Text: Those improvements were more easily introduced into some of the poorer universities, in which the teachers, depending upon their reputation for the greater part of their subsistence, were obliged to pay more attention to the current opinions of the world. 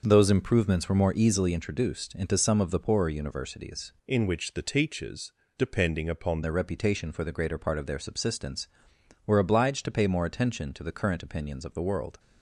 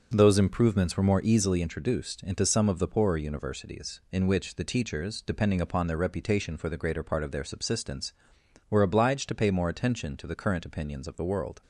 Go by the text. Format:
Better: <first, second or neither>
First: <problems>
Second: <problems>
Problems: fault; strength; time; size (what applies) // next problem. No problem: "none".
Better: second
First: starts louder than the rest; until 1.0 s; 6.5 dB // changes voice from "in" to "upon"; from 4.0 to 6.4 s; 2.4 s long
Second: starts louder than the rest; until 1.1 s; 6.5 dB